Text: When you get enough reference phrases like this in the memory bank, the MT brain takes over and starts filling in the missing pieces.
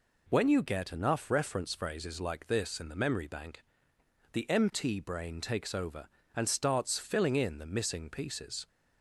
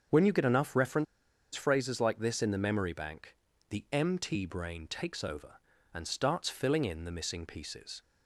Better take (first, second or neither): first